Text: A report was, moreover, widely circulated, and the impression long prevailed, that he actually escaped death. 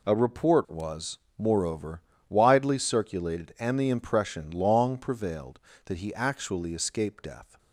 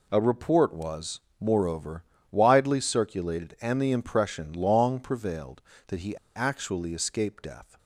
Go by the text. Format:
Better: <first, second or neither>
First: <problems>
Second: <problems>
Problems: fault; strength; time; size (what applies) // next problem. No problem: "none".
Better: first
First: none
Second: pauses between "he" and "actually"; slight; at 6.1 s; 0.19 s long